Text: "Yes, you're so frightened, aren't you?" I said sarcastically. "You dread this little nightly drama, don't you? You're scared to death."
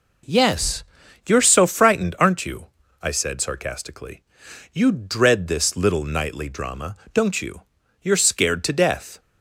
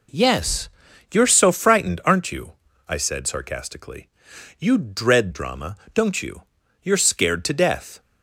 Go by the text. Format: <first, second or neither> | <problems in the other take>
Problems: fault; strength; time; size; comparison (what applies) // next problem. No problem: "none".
first | skips "this little nightly"; at 5.3 s